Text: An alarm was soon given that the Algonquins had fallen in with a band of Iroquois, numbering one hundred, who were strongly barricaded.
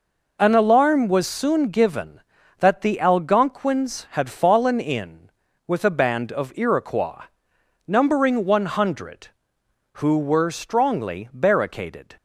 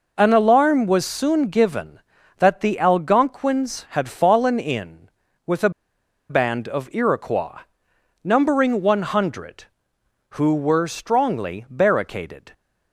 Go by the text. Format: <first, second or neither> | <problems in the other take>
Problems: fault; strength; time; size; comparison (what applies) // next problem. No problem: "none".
first | pauses between "a" and "band"; noticeable; at 5.6 s; 0.59 s long